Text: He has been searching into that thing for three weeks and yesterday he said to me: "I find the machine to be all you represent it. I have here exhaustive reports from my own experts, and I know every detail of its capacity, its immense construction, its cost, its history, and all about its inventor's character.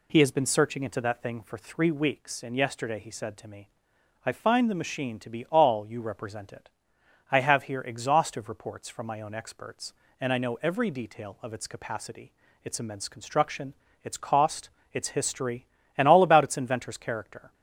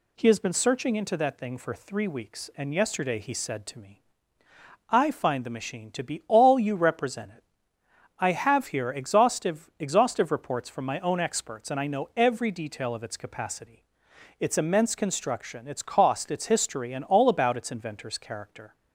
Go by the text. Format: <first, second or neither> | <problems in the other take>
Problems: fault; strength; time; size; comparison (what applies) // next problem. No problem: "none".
first | says "exhaustive" twice; at 9.7 s